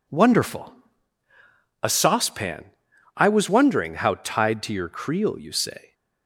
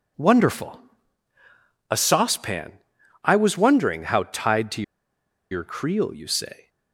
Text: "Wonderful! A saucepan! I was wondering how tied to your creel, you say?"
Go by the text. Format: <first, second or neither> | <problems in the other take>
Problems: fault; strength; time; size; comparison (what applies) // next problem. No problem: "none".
first | pauses between "to" and "your"; noticeable; at 4.8 s; 0.69 s long